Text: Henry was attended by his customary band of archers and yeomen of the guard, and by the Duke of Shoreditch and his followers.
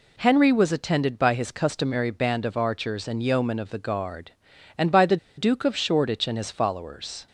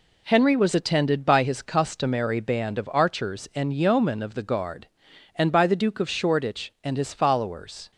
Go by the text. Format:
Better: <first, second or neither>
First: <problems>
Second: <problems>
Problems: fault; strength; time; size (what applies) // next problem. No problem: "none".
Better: second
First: pauses between "the" and "Duke"; slight; at 5.1 s; 0.21 s long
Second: none